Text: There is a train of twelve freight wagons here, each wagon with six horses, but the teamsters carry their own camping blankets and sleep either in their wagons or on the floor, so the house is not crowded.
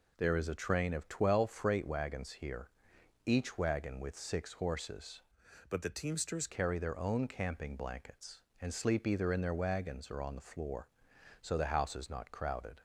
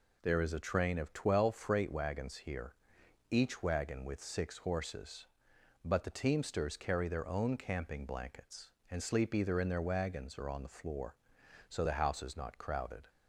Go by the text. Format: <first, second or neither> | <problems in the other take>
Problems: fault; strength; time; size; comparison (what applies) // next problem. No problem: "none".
second | changes voice from "but" to "teamsters"; from 5.6 to 6.4 s; 0.8 s long